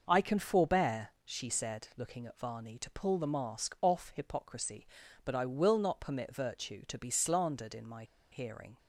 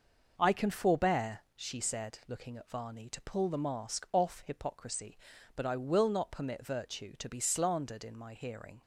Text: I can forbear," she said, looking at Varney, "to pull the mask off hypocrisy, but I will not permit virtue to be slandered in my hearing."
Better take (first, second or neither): second